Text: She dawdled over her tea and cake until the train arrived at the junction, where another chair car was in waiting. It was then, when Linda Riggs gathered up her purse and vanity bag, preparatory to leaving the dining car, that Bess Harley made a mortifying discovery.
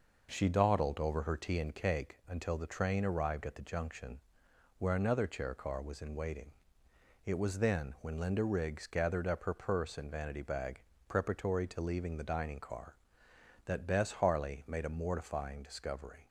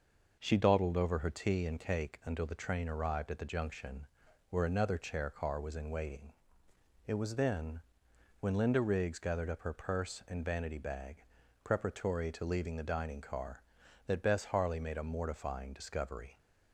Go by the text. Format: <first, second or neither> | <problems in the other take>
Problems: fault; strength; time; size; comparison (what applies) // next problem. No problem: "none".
neither | none